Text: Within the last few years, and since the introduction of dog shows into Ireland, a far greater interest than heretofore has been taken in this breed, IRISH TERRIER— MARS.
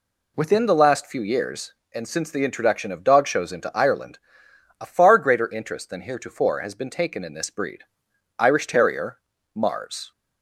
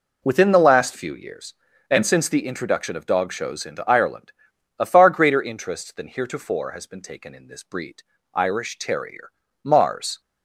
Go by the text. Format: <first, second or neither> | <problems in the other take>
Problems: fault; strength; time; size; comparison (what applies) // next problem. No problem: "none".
neither | none